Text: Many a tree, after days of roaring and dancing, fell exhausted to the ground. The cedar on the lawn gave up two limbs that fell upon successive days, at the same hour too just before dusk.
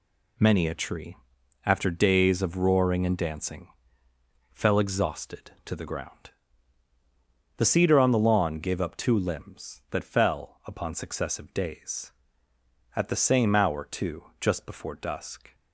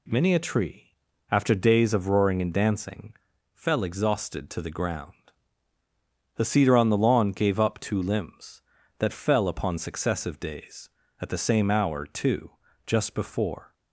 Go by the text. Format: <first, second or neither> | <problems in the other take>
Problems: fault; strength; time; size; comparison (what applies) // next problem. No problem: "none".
first | pauses between "too" and "just"; slight; at 12.5 s; 0.34 s long; slight in the first // stops before "dusk"; at 13.7 s